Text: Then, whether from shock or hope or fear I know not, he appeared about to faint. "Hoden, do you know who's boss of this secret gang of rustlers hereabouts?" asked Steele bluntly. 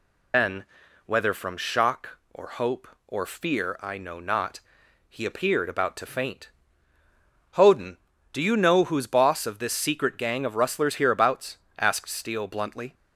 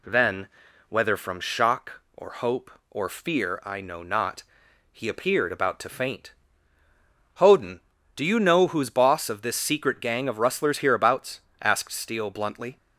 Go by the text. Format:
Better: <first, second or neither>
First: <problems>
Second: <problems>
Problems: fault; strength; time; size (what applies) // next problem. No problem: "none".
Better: second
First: loses the start of "Then"; at 0.3 s; 130 ms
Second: none